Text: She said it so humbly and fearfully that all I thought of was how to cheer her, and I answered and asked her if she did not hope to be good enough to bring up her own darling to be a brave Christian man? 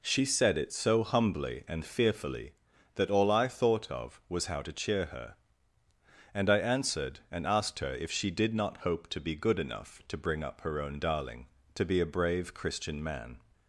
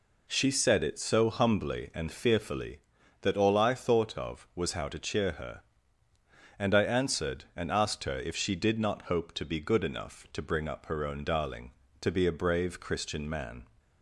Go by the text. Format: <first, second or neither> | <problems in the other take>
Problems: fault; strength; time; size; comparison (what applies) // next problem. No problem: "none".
neither | none